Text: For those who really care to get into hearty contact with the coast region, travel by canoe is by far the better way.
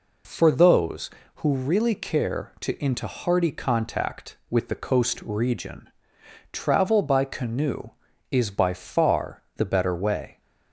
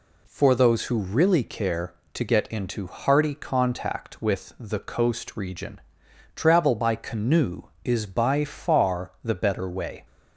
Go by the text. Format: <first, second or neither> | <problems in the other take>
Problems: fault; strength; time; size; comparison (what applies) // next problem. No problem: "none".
second | skips "get"; at 2.7 s